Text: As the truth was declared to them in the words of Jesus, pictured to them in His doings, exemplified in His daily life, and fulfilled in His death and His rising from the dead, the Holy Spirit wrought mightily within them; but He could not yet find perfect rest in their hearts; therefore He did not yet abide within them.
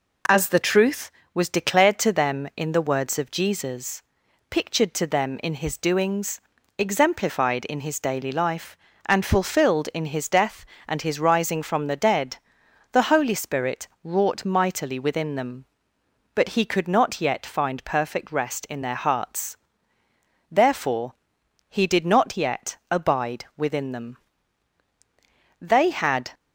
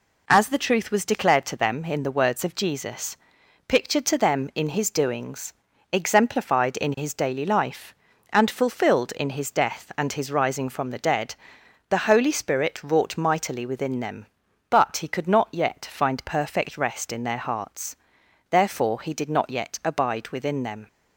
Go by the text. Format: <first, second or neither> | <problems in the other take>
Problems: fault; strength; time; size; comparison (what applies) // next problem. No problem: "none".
second | pauses between "Spirit" and "wrought"; slight; at 13.8 s; 0.16 s long // pauses between "therefore" and "He"; noticeable; at 21.1 s; 0.54 s long // pauses between "abide" and "within"; slight; at 23.4 s; 0.16 s long // goes on to say "They had"; noticeable; from 25.5 s on; 0.72 s long